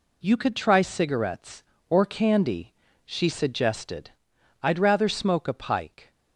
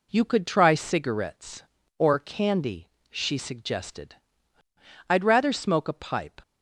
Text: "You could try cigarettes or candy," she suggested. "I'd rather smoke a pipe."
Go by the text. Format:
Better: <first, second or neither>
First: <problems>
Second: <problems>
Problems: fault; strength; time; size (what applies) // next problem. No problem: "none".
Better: second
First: says "pike" for "pipe"; at 5.5 s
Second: none